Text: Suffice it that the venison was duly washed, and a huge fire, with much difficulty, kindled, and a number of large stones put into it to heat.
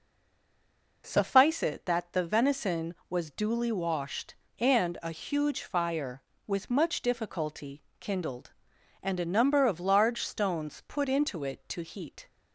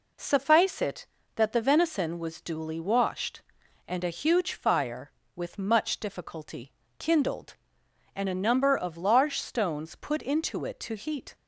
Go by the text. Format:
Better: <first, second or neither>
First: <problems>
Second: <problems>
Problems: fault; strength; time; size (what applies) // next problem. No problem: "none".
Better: second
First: stays silent before the first word; until 1.0 s; 1.0 s long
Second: none